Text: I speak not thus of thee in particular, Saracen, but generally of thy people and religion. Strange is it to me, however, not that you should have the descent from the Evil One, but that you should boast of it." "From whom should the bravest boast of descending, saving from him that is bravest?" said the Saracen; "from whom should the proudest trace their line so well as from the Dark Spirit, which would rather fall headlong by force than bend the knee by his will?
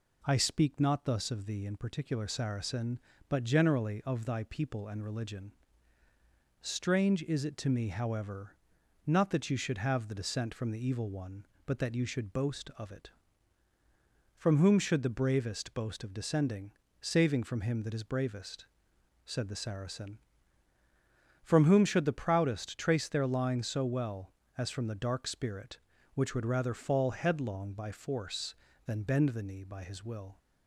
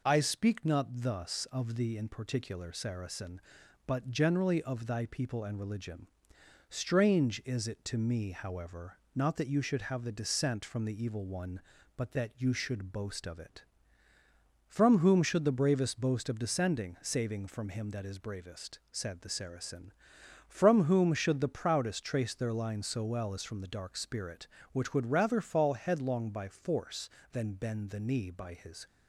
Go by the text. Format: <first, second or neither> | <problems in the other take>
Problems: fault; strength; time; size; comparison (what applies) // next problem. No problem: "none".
first | stops before "will"; at 28.8 s